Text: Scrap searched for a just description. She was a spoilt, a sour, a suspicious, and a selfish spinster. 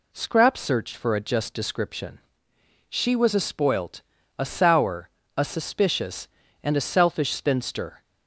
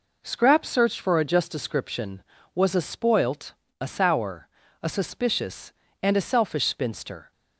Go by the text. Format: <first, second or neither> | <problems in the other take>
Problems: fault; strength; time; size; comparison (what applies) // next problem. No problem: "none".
first | skips "She"; at 2.3 s